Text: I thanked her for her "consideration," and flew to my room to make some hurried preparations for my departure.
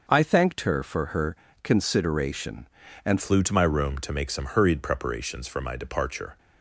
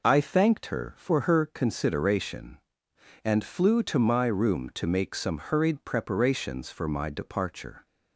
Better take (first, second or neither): second